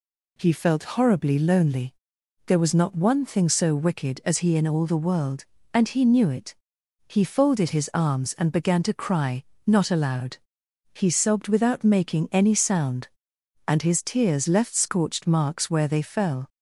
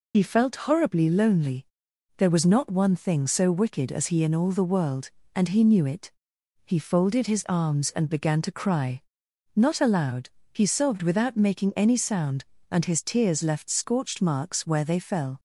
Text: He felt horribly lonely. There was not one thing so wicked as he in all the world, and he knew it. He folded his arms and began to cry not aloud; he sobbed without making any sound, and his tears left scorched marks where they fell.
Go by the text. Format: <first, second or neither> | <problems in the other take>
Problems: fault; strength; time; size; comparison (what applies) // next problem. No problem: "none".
first | loses the start of "He"; at 0.1 s; 75 ms // pauses between "cry" and "not"; noticeable; at 9.0 s; 0.54 s long; slight in the first